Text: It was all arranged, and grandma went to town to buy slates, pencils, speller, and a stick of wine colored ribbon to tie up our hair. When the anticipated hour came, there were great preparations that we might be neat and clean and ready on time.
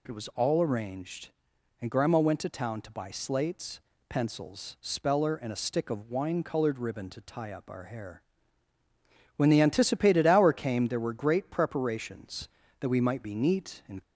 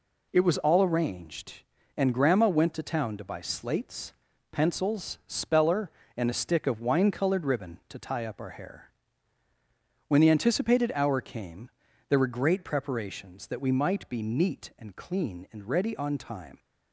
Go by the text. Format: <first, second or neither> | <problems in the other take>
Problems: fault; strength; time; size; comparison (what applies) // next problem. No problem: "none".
second | stops before "clean and ready on time"; at 14.0 s